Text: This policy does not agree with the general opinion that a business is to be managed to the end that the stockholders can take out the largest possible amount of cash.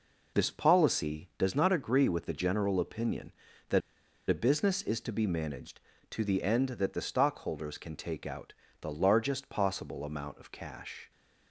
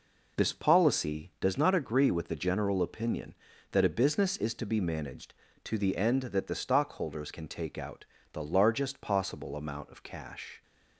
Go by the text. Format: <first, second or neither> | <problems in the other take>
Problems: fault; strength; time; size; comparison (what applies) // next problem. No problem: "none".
second | pauses between "that" and "a"; noticeable; at 3.8 s; 0.49 s long // pauses between "out" and "the"; slight; at 8.5 s; 0.26 s long; slight in the second